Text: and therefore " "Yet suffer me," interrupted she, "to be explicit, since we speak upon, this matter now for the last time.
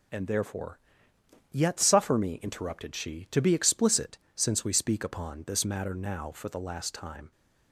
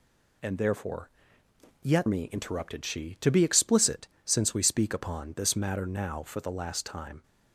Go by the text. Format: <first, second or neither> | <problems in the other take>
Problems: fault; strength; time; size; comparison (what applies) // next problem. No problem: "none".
first | skips "suffer"; at 2.0 s